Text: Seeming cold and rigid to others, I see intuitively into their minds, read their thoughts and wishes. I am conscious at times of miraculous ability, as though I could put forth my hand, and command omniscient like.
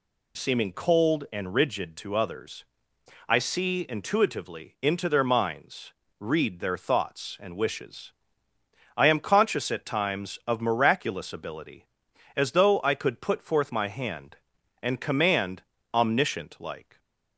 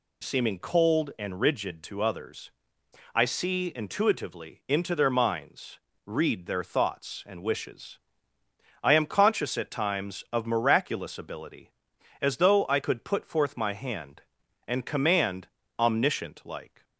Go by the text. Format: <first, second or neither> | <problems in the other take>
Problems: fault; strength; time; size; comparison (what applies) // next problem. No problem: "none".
neither | pauses between "command" and "omniscient"; slight; the same in both